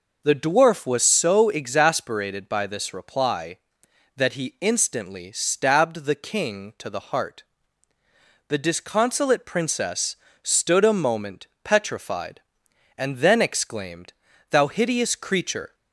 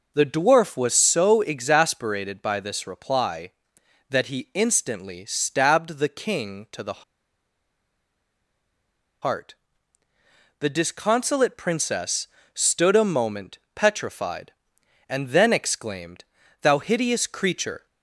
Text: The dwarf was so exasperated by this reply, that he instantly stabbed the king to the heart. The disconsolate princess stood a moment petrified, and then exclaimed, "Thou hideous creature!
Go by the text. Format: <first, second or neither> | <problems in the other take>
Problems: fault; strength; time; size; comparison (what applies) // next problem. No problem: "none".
first | pauses between "the" and "heart"; strong; at 7.0 s; 2.1 s long // pauses between "princess" and "stood"; slight; at 12.2 s; 0.26 s long; slight in the first // pauses between "moment" and "petrified"; slight; at 13.5 s; 0.16 s long; slight in the first